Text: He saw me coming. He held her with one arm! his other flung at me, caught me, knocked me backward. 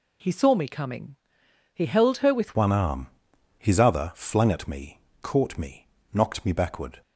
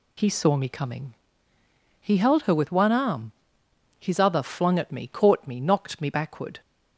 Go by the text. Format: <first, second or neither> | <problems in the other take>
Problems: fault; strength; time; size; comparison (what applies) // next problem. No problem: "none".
second | changes voice at "one"; from 2.5 s on; 4.5 s long